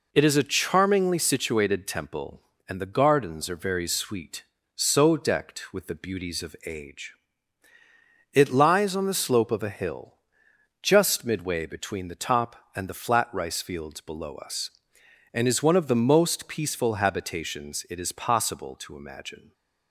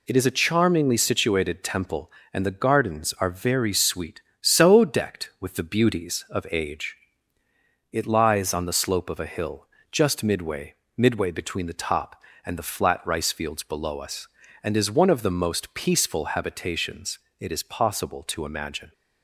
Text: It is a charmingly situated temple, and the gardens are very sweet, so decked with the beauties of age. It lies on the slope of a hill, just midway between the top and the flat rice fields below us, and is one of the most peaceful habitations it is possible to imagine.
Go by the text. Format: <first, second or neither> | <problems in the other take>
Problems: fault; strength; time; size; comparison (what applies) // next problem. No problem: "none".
first | says "midway" twice; at 10.9 s // pauses between "habitations" and "it"; slight; at 17.1 s; 0.22 s long